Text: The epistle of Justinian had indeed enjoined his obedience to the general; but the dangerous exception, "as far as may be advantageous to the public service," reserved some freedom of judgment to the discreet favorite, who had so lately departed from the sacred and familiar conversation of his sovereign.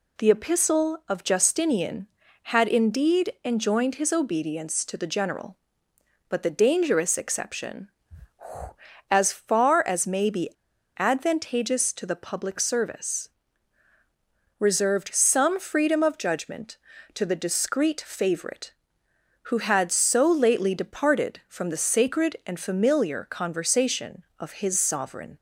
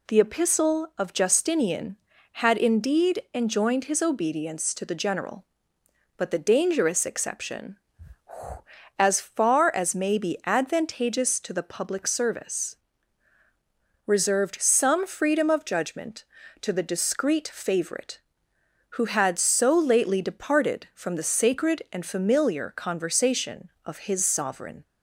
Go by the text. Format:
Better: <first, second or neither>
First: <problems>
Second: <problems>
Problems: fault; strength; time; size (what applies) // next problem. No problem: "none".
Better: second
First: pauses between "be" and "advantageous"; noticeable; at 10.4 s; 0.49 s long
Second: none